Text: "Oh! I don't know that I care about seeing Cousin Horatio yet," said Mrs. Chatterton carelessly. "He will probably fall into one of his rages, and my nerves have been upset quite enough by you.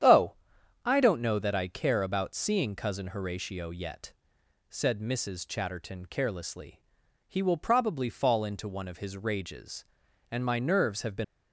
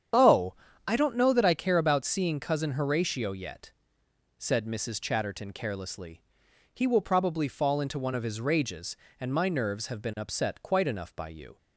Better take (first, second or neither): second